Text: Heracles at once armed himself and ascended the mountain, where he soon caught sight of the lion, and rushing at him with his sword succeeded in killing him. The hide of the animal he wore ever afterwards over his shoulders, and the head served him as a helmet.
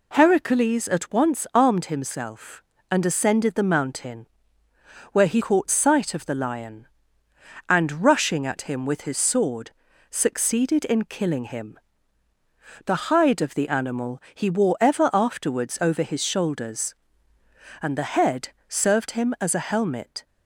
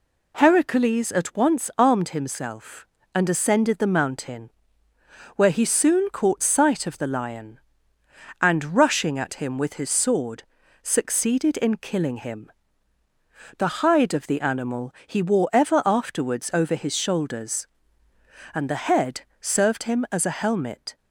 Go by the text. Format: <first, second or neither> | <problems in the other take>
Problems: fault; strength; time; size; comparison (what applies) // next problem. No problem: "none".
second | skips "soon"; at 5.3 s // pauses between "sword" and "succeeded"; at 9.7 s; 0.38 s long; also in the second // pauses between "head" and "served"; slight; at 18.4 s; 0.18 s long; slight in the second